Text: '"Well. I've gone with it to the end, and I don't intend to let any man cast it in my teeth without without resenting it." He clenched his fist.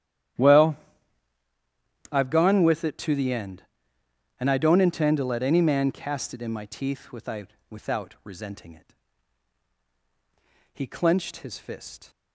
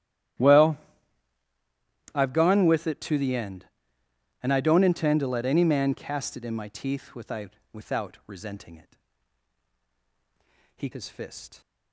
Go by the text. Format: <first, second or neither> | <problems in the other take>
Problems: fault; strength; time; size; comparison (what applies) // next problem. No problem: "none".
first | starts louder than the rest; strong; until 2.7 s; 12.5 dB; strong in the first // pauses between "without" and "without"; slight; at 7.5 s; 0.22 s long; slight in the first // skips "clenched"; at 10.9 s